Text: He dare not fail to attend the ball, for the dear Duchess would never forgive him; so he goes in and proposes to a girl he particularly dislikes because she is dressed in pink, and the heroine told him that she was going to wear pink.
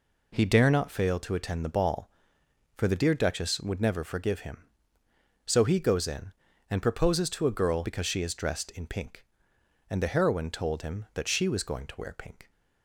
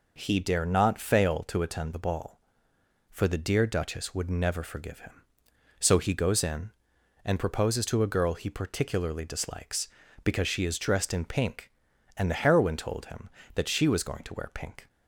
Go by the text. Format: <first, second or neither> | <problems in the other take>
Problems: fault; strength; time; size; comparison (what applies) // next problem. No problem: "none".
second | skips "he particularly dislikes"; at 7.8 s